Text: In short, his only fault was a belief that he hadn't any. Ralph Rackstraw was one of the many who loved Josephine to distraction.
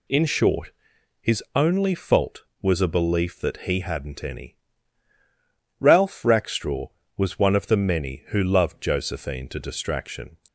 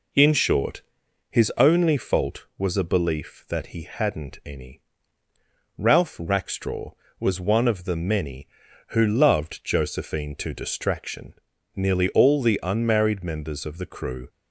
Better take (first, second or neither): first